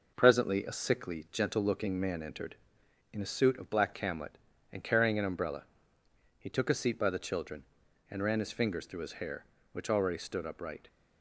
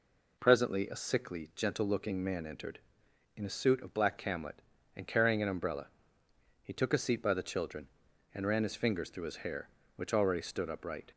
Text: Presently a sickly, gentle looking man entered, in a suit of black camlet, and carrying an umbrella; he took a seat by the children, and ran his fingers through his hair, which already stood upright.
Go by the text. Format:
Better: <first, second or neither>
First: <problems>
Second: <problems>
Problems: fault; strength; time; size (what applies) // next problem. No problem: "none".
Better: second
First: gets quieter; noticeable; throughout; 4.5 dB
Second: none